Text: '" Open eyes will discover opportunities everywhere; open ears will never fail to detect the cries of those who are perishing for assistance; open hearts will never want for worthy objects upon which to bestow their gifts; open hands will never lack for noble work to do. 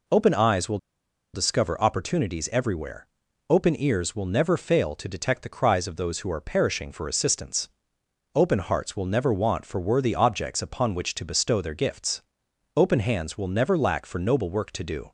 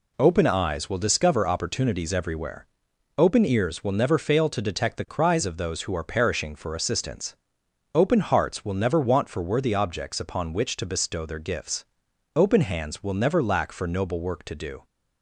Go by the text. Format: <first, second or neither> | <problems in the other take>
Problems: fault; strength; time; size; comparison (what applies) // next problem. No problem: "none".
second | pauses between "will" and "discover"; noticeable; at 0.7 s; 0.56 s long